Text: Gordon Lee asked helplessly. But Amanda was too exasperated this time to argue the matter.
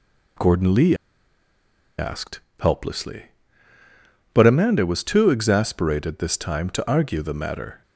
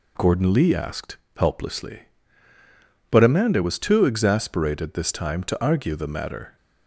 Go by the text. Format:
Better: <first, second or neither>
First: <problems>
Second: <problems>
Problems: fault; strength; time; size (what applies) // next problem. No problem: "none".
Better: second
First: pauses between "Lee" and "asked"; at 0.9 s; 1.0 s long // pauses between "asked" and "helplessly"; slight; at 2.3 s; 0.20 s long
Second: pauses between "asked" and "helplessly"; slight; at 1.1 s; 0.20 s long